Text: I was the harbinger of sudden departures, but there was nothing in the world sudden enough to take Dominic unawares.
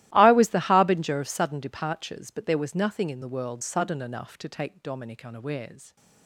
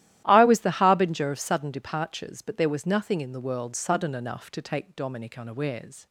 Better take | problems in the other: second | gets quieter; strong; throughout; 20.5 dB // starts louder than the rest; strong; until 1.1 s; 15.5 dB; strong in the second

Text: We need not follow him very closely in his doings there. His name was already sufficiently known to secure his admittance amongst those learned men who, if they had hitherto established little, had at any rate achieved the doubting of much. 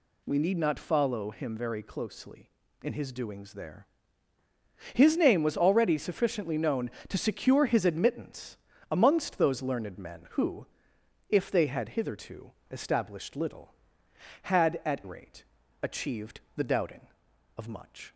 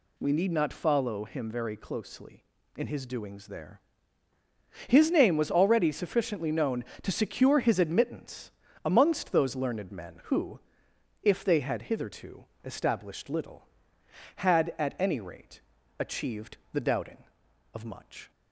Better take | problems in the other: second | pauses between "admittance" and "amongst"; slight; at 8.5 s; 0.34 s long; slight in the second // pauses between "hitherto" and "established"; slight; at 12.5 s; 0.20 s long; slight in the second // skips "any"; at 15.0 s // pauses between "rate" and "achieved"; at 15.4 s; 0.38 s long; also in the second // pauses between "achieved" and "the"; slight; at 16.3 s; 0.16 s long; slight in the second

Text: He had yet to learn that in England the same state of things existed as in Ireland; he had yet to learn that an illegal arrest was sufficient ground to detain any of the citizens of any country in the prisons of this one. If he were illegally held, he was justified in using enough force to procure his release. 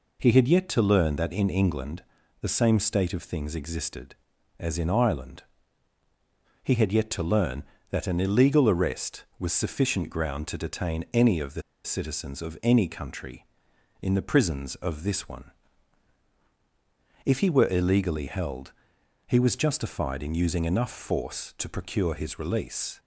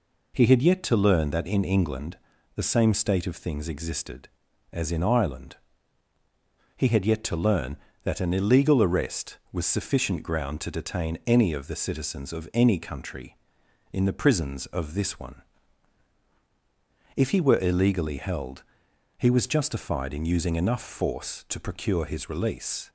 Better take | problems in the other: second | pauses between "England" and "the"; at 2.0 s; 0.38 s long; also in the second // pauses between "the" and "citizens"; slight; at 11.6 s; 0.23 s long

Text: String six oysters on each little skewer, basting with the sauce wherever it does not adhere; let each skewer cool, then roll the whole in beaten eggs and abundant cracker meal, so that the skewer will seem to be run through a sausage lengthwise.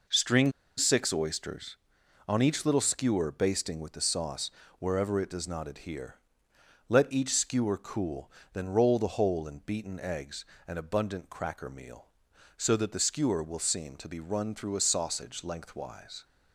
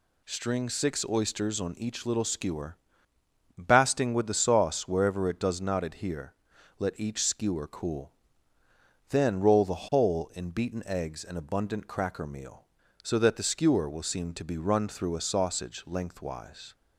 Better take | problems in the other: second | pauses between "String" and "six"; slight; at 0.5 s; 0.27 s long // pauses between "sauce" and "wherever"; slight; at 4.4 s; 0.30 s long

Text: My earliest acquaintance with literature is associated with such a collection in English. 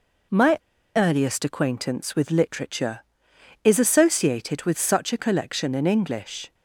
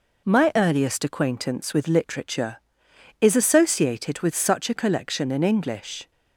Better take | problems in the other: second | pauses between "My" and "earliest"; at 0.5 s; 0.36 s long

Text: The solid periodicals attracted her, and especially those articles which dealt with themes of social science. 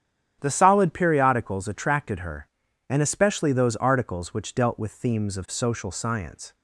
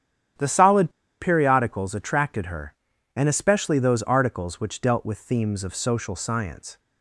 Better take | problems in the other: first | starts louder than the rest; strong; until 1.6 s; 9.5 dB; strong in the first // pauses between "solid" and "periodicals"; slight; at 0.8 s; 0.30 s long

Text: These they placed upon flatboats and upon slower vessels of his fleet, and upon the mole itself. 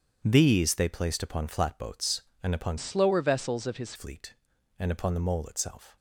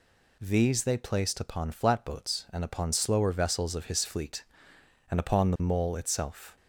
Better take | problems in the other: second | starts louder than the rest; strong; until 1.2 s; 8 dB // changes voice from "slower" to "his"; from 2.7 to 3.9 s; 1.2 s long

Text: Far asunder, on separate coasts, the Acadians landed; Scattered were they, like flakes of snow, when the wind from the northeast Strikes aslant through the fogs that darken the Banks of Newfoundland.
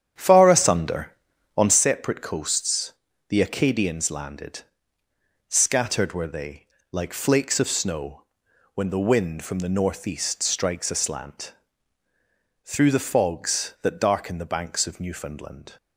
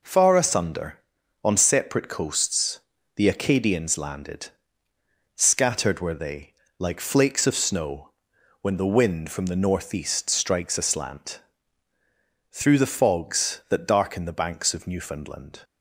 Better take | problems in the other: second | starts louder than the rest; strong; until 1.9 s; 9 dB // pauses between "aslant" and "through"; at 11.5 s; 1.1 s long; also in the second

